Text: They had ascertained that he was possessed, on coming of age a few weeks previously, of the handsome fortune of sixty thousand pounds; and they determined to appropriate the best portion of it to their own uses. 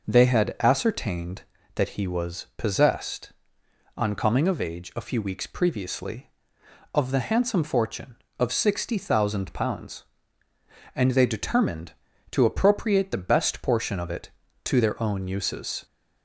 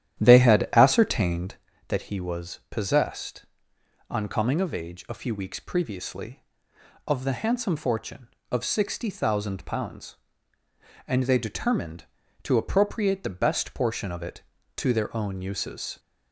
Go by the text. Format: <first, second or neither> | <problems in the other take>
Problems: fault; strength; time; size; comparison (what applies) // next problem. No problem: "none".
first | starts louder than the rest; strong; until 1.6 s; 11 dB